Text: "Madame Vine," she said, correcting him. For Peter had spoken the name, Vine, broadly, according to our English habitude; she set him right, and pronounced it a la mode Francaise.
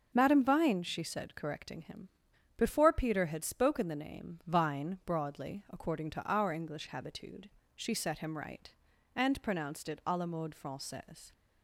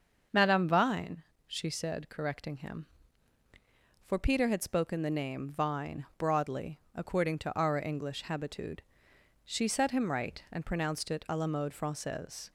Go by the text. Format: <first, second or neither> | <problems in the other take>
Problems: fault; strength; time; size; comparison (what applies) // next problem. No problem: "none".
second | starts louder than the rest; until 1.1 s; 6 dB; also in the second // says "Before" for "For"; at 2.5 s